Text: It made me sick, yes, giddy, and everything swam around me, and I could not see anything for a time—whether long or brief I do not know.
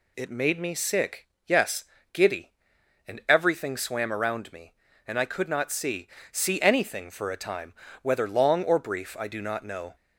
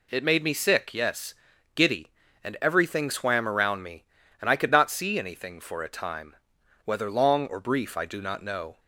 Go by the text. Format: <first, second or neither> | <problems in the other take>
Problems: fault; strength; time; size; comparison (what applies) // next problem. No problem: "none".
second | says "see" twice; at 6.3 s